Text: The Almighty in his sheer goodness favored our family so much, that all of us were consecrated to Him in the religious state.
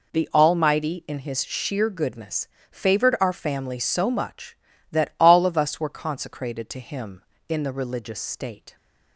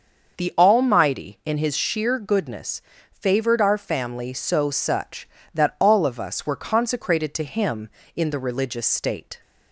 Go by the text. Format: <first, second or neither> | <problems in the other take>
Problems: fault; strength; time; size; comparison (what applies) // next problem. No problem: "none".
first | starts louder than the rest; until 1.4 s; 6.5 dB // pauses between "goodness" and "favored"; slight; at 2.8 s; 0.28 s long; slight in the first // says "such" for "much"; at 4.7 s